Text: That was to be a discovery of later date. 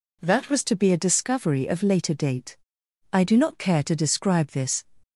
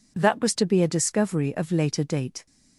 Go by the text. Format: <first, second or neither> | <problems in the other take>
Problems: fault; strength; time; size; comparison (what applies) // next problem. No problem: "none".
second | goes on to say "I do not care to describe this"; strong; from 3.1 s on; 1.7 s long